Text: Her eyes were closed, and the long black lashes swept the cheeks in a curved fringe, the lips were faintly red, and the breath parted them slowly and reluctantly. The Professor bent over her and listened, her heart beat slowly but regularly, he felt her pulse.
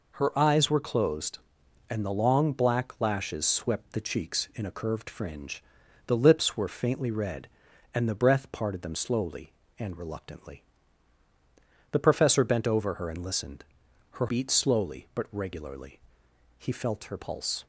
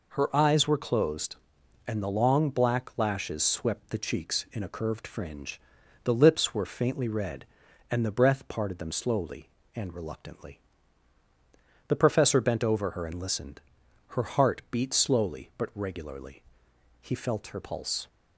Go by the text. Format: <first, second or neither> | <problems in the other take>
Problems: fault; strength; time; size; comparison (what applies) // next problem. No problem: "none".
second | skips "heart"; at 14.2 s